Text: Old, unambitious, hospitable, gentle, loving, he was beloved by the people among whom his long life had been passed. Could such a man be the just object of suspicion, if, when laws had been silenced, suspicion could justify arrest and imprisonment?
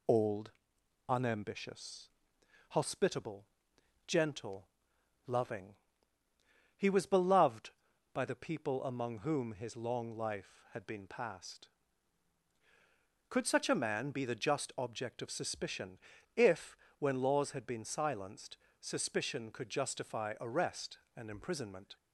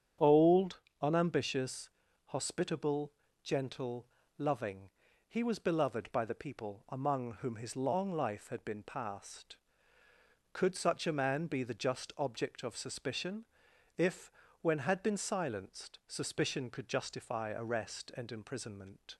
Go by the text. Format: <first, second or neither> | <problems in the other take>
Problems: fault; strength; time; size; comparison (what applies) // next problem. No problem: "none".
first | starts louder than the rest; strong; until 1.4 s; 8.5 dB // skips "laws"; at 14.7 s